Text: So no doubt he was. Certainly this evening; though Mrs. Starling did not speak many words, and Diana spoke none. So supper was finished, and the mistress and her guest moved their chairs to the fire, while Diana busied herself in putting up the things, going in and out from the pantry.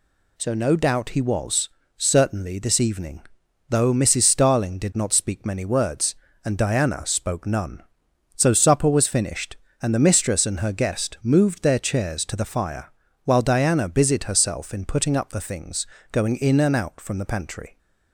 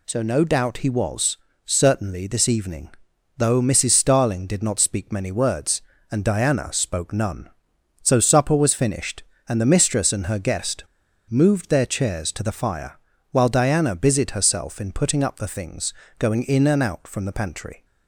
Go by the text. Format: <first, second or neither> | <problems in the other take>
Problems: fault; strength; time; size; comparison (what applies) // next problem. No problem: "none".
first | pauses between "guest" and "moved"; noticeable; at 10.8 s; 0.46 s long